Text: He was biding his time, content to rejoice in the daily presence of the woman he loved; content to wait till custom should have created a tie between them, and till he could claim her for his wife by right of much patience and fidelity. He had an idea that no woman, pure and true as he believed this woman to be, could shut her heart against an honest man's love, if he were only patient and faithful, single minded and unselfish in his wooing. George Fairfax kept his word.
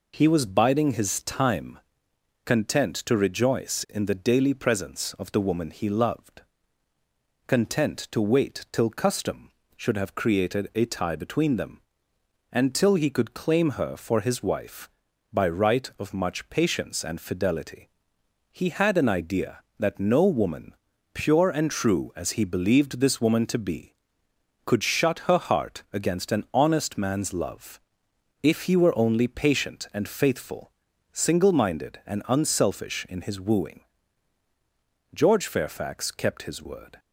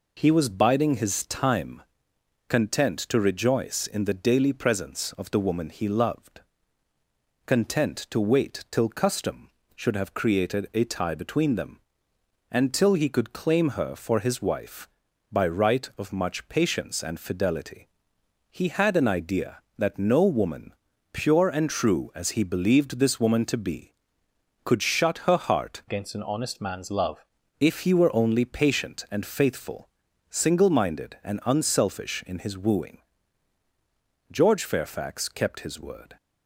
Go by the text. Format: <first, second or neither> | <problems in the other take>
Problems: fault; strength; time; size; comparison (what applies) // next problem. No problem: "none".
first | changes voice from "against" to "love"; from 25.8 to 27.2 s; 1.4 s long